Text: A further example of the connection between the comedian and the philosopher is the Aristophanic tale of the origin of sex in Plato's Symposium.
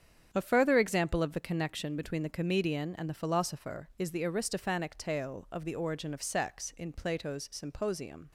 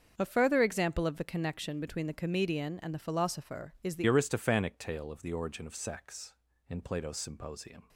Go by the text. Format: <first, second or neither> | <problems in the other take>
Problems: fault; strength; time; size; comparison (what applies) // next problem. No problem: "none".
first | starts louder than the rest; until 1.1 s; 6.5 dB; strong in the first // changes voice at "Aristophanic"; from 4.0 s on; 3.8 s long